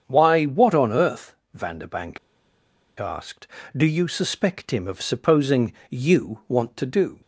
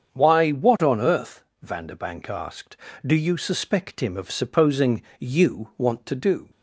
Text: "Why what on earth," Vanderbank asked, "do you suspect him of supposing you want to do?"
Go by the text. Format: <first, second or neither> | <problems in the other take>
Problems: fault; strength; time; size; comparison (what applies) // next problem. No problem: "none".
second | starts louder than the rest; strong; until 1.0 s; 7 dB; strong in the second // pauses between "Vanderbank" and "asked"; noticeable; at 2.1 s; 0.80 s long // pauses between "supposing" and "you"; slight; at 5.7 s; 0.18 s long; slight in the second